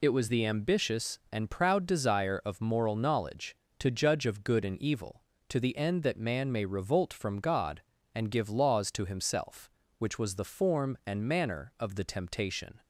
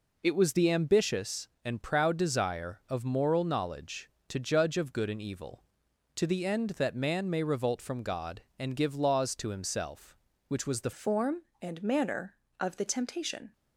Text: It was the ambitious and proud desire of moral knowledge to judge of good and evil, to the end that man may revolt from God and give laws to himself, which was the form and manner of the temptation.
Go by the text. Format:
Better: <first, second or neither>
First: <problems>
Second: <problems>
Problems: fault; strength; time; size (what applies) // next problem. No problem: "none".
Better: first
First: none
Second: changes voice at "form"; from 10.9 s on; 2.6 s long